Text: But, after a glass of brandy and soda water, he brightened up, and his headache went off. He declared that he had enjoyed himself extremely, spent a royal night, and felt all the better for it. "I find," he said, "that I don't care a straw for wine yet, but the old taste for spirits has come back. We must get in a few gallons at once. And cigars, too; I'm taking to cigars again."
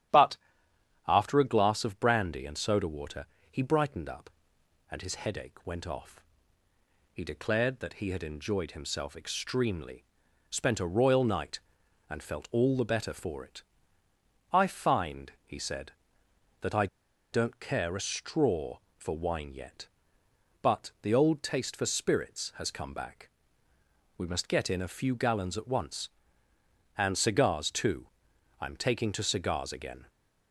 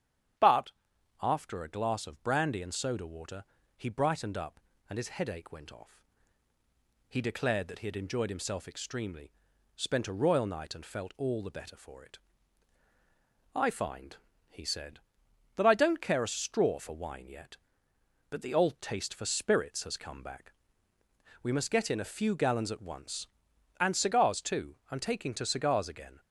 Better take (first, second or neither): second